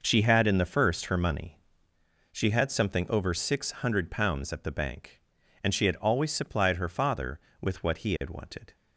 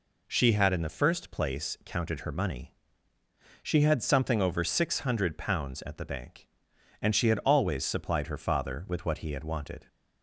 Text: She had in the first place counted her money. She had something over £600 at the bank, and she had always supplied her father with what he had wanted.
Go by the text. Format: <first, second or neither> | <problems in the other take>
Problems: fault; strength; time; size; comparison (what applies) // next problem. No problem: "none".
second | skips "place counted"; at 1.0 s